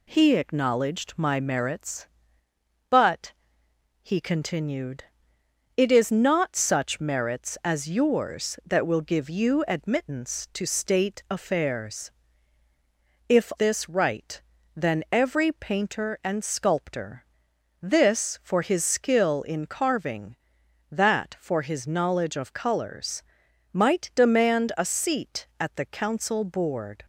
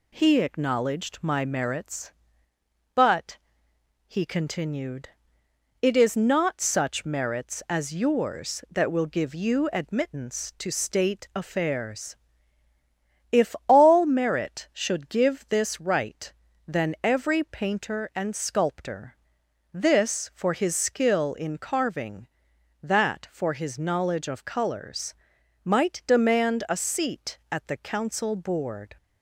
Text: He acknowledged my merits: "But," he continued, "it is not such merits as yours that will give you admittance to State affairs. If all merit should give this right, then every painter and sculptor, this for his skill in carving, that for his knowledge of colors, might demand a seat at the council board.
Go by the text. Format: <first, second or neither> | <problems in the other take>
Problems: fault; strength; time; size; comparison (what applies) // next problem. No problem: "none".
second | skips "all merit should give"; at 13.5 s